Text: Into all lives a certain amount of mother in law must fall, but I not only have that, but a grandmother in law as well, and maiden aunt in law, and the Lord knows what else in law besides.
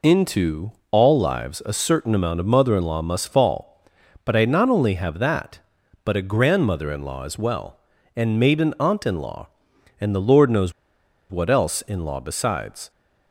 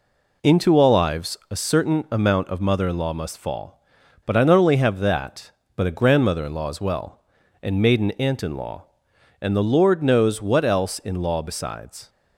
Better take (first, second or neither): second